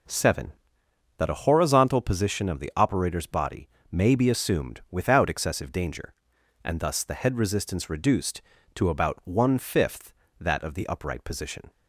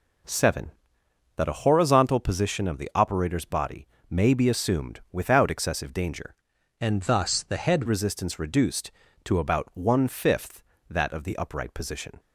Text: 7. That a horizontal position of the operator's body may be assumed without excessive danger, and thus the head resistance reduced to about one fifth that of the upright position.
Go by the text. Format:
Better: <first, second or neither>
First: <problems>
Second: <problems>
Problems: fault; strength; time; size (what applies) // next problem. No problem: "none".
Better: first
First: pauses between "body" and "may"; slight; at 3.6 s; 0.22 s long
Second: pauses between "body" and "may"; slight; at 3.8 s; 0.22 s long // changes voice from "and" to "head"; from 6.8 to 7.8 s; 1.0 s long